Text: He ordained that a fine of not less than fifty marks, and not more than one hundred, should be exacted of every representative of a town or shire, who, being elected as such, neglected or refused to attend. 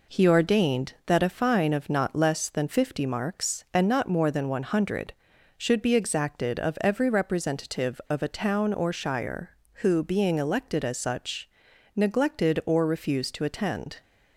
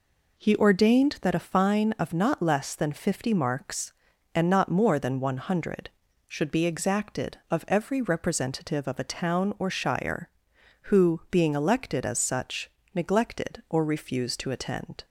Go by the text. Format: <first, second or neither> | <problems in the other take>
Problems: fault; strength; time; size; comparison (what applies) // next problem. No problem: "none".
neither | none